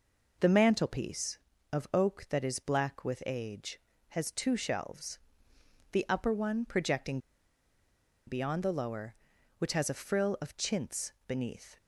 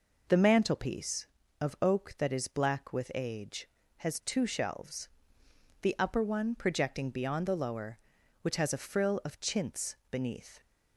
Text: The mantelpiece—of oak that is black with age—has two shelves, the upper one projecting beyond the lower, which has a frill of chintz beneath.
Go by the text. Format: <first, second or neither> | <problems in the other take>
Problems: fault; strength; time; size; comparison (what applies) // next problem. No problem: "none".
second | pauses between "projecting" and "beyond"; at 7.1 s; 1.0 s long